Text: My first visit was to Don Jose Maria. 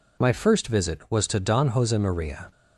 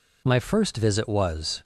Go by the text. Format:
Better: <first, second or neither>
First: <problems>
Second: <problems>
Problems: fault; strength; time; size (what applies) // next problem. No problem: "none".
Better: first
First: none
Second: stops before "to Don Jose Maria"; at 1.6 s